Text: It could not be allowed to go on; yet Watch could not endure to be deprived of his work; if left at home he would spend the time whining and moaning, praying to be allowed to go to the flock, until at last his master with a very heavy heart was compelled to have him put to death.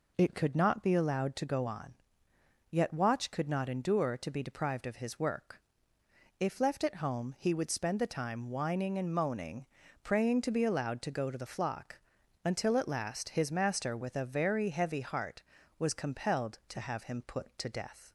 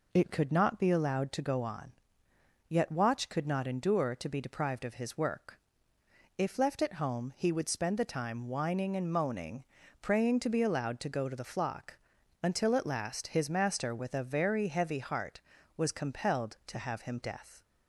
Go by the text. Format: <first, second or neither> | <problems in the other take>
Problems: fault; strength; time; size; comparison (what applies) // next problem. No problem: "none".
first | skips "put to"; at 17.2 s